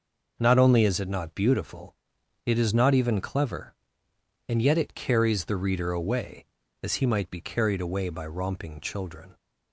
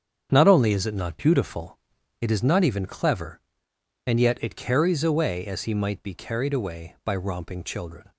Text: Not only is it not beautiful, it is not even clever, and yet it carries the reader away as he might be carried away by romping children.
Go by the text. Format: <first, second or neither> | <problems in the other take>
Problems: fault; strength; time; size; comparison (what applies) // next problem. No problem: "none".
first | starts louder than the rest; strong; until 1.3 s; 7.5 dB // skips "the reader"; at 5.0 s